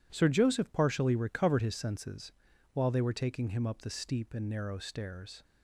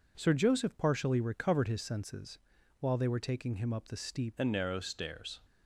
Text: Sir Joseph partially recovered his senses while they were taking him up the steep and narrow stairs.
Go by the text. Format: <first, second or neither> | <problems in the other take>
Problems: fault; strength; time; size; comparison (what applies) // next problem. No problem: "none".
first | pauses between "senses" and "while"; at 2.3 s; 0.42 s long; also in the first // changes voice at "and"; from 4.3 s on; 1.0 s long